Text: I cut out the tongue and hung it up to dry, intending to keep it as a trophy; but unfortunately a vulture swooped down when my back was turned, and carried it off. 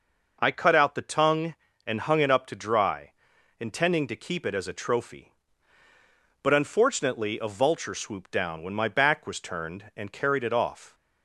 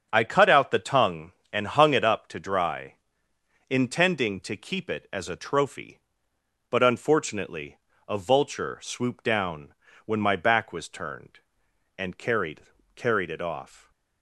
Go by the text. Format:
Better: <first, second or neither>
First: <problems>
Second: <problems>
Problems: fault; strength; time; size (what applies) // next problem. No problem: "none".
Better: first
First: none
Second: starts louder than the rest; strong; until 1.1 s; 7.5 dB // pauses between "unfortunately" and "a"; slight; at 7.7 s; 0.32 s long // pauses between "down" and "when"; slight; at 9.7 s; 0.30 s long // says "carried" twice; at 12.9 s